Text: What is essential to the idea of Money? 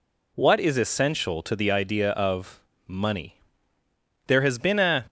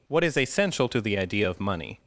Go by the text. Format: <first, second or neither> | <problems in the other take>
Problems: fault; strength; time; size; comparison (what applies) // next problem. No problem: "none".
second | pauses between "of" and "Money"; slight; at 2.6 s; 0.26 s long // goes on to say "There has been a"; noticeable; from 4.2 s on; 0.80 s long